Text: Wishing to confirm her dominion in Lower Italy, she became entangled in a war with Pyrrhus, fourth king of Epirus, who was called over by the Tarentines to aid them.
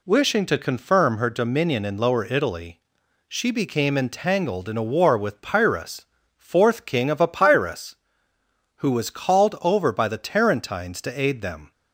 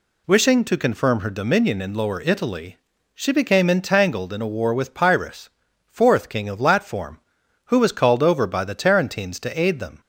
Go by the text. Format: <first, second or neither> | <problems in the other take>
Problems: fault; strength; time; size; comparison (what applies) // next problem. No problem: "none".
first | says "Latform" for "Epirus"; at 6.6 s